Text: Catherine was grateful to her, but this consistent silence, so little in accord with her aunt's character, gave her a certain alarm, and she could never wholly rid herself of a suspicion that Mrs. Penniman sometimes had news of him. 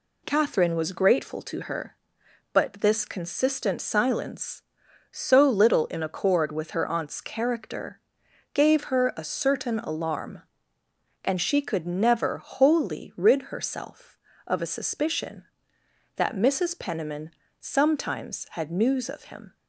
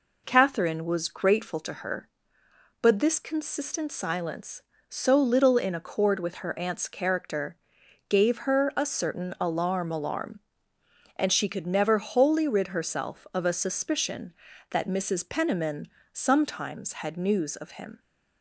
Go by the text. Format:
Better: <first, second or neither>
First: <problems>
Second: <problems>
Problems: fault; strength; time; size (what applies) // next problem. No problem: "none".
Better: first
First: pauses between "Penniman" and "sometimes"; slight; at 17.3 s; 0.30 s long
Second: says "alarm" twice; at 9.9 s // pauses between "Penniman" and "sometimes"; slight; at 15.8 s; 0.22 s long